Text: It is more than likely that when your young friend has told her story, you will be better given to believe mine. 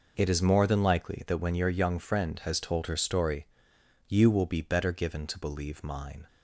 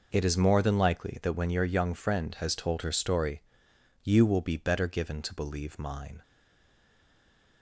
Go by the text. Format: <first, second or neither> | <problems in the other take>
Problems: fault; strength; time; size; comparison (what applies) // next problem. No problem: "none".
first | stays silent after the last word; noticeable; from 6.2 s on; 1.4 s long